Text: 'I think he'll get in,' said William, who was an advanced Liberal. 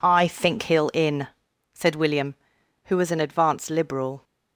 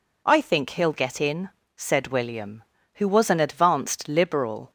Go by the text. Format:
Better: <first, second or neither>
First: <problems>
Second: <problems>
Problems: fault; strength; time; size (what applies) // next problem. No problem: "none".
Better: second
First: skips "get"; at 0.9 s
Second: none